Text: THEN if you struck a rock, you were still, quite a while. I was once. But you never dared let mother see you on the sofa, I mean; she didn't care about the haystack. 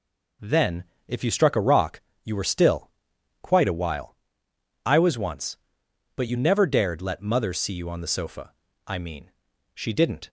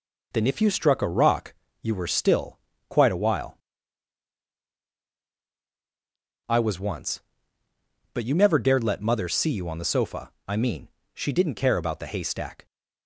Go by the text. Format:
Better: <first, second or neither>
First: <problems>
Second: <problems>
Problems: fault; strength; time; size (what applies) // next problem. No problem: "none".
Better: second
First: pauses between "THEN" and "if"; slight; at 0.8 s; 0.22 s long // stops before "care about the haystack"; at 10.2 s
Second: none